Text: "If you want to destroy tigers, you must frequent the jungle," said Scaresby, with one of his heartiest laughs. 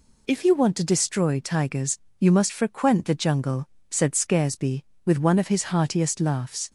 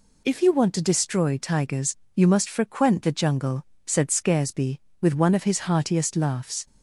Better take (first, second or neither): neither